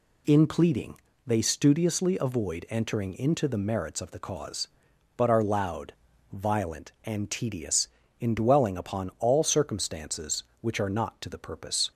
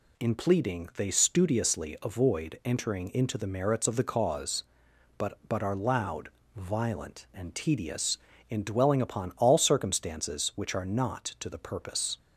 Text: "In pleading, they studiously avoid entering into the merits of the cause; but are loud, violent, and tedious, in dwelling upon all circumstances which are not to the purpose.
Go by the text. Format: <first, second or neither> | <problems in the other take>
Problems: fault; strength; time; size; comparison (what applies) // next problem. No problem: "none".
first | says "but" twice; at 5.4 s